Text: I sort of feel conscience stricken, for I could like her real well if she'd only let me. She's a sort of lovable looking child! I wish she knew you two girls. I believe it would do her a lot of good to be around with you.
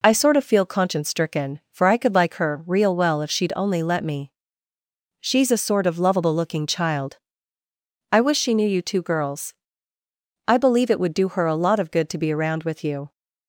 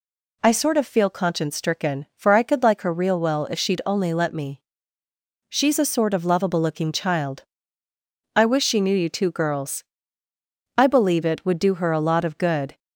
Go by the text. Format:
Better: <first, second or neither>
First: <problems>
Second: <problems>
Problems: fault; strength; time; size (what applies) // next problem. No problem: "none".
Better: first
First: none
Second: stops before "to be around with you"; at 12.7 s